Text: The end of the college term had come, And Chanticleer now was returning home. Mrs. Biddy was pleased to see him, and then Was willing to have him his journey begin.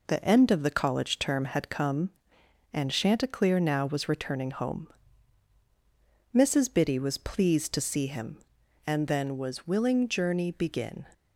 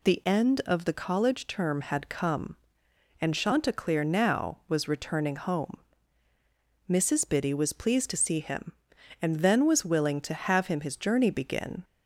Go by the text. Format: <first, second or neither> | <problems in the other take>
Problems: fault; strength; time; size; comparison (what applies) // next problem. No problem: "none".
second | skips "to have him his"; at 10.0 s